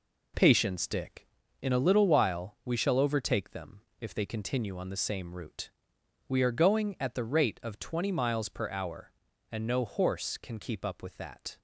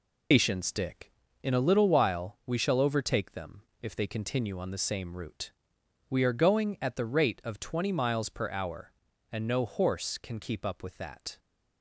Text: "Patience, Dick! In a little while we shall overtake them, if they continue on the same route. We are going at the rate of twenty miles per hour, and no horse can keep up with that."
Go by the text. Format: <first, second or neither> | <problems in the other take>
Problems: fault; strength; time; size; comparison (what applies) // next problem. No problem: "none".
first | loses the start of "Patience"; at 0.3 s; 120 ms